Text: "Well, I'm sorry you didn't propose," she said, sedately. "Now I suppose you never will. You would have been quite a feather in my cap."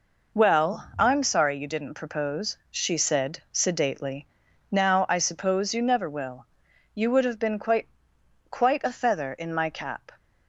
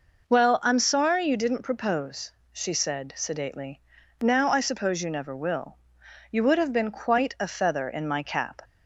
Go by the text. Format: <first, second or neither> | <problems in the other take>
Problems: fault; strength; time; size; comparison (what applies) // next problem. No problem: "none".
second | says "quite" twice; at 8.4 s